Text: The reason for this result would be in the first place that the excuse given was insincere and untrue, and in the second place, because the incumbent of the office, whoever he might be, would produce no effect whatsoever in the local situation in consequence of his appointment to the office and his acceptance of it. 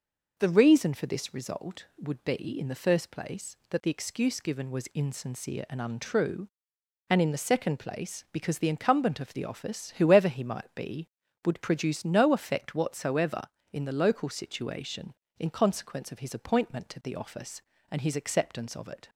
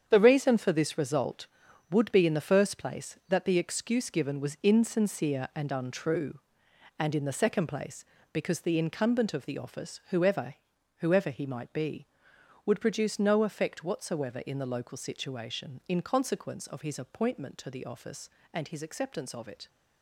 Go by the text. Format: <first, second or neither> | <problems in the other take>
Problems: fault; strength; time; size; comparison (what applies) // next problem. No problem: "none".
first | starts louder than the rest; strong; until 1.0 s; 8 dB // says "whoever" twice; at 10.9 s